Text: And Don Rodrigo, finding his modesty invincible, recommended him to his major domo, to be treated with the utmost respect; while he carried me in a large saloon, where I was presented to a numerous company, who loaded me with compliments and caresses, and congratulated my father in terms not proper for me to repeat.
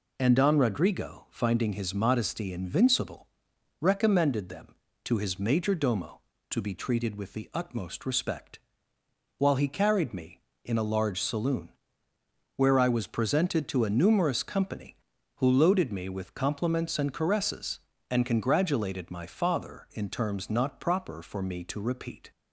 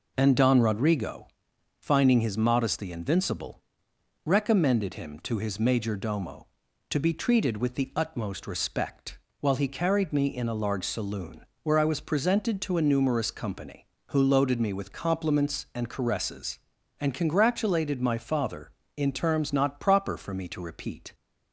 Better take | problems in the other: second | says "them" for "him"; at 4.4 s

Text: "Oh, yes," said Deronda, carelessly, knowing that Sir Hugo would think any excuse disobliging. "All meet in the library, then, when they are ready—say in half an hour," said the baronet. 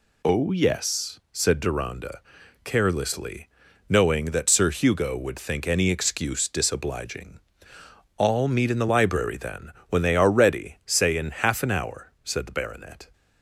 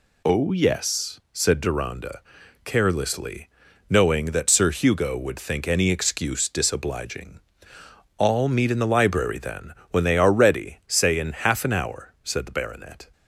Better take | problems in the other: neither | none

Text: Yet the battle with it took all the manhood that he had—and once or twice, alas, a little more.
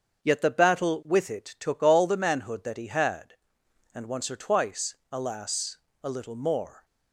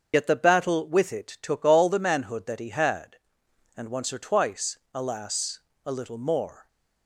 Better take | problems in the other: first | loses the start of "Yet"; at 0.1 s; 55 ms // starts louder than the rest; until 1.1 s; 7 dB; also in the first

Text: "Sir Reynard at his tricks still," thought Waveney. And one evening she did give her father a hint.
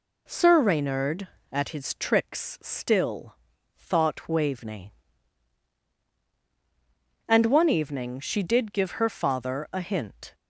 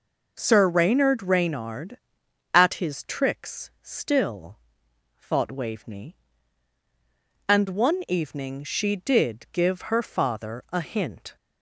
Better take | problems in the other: first | says "Reynard" twice; at 1.2 s

